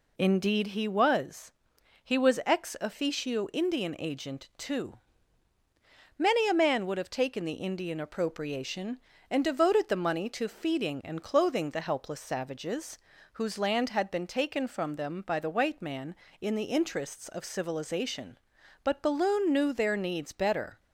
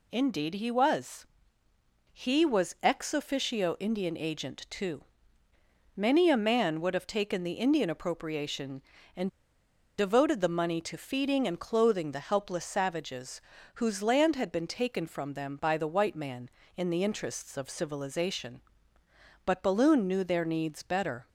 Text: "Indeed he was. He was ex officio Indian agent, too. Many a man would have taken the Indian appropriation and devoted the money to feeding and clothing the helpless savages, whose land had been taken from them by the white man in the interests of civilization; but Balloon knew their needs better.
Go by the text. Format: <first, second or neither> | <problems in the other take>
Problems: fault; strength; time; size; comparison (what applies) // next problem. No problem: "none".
first | pauses between "and" and "devoted"; noticeable; at 9.2 s; 0.70 s long